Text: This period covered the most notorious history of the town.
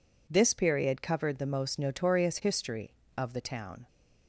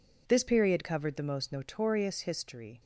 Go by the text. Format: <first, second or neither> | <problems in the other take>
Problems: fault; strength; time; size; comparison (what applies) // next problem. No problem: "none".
first | stops before "of the town"; at 2.8 s